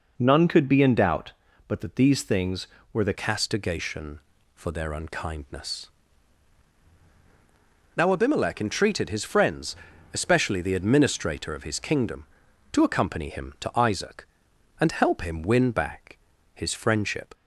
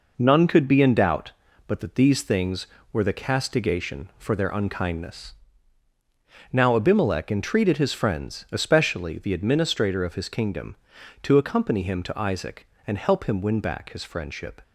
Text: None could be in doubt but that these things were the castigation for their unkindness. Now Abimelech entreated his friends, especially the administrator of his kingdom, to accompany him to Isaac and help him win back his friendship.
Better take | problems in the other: second | changes voice at "castigation"; from 3.1 s on; 14.2 s long // pauses between "back" and "his"; slight; at 16.1 s; 0.36 s long

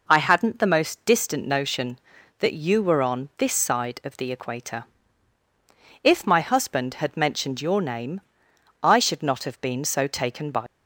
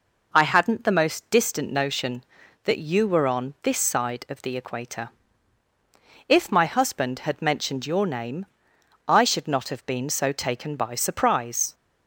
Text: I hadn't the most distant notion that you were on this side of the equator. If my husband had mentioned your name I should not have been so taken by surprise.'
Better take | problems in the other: second | pauses between "name" and "I"; noticeable; at 8.2 s; 0.62 s long; noticeable in the second // stops before "surprise"; at 10.6 s

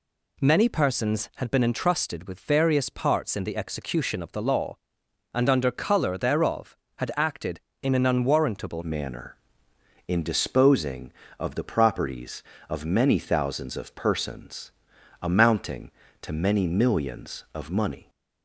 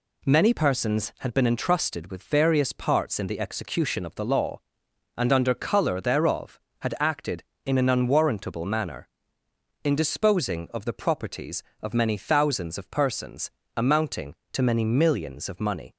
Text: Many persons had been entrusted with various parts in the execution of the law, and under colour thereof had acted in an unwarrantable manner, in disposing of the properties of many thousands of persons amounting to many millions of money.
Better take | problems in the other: second | changes voice at "manner"; from 8.8 s on; 9.2 s long // pauses between "persons" and "amounting"; noticeable; at 14.7 s; 0.50 s long; slight in the second

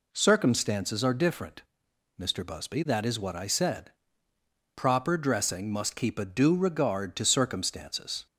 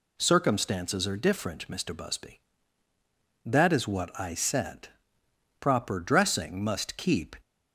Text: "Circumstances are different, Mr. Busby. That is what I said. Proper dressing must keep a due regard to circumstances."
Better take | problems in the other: first | stops before "a due regard to circumstances"; at 7.4 s

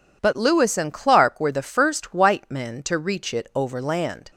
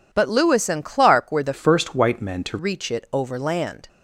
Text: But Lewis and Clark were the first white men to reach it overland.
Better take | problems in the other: first | changes voice from "first" to "to"; from 1.5 to 2.5 s; 1.0 s long

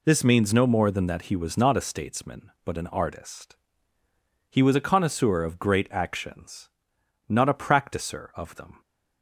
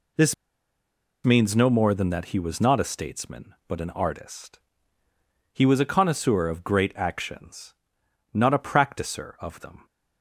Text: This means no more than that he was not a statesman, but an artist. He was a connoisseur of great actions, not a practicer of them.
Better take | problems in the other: first | pauses between "This" and "means"; noticeable; at 0.3 s; 0.90 s long

